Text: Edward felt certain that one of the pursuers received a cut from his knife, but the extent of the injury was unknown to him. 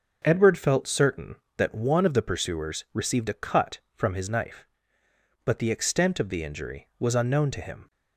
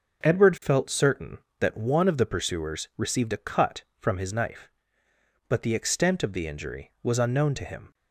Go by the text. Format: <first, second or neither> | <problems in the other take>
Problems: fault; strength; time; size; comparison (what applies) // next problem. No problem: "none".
neither | starts louder than the rest; the same in both